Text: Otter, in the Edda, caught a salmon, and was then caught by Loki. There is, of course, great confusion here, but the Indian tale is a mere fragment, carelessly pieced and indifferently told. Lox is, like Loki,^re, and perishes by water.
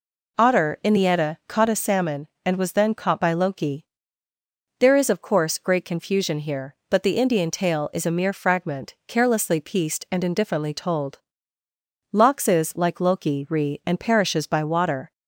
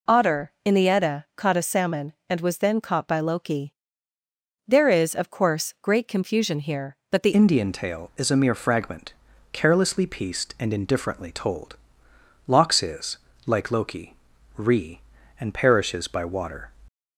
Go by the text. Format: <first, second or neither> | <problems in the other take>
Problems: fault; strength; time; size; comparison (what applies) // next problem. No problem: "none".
first | changes voice at "Indian"; from 7.3 s on; 9.4 s long